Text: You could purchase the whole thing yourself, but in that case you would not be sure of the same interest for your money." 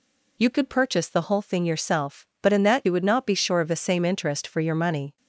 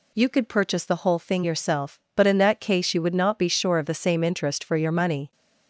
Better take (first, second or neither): second